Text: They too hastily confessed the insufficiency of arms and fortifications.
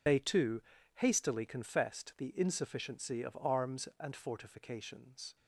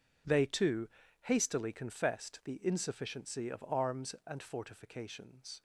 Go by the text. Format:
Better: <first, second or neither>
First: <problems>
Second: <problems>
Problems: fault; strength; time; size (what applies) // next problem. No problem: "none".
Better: second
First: loses the start of "They"; at 0.0 s; 80 ms // pauses between "too" and "hastily"; slight; at 0.6 s; 0.34 s long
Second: pauses between "too" and "hastily"; slight; at 0.8 s; 0.34 s long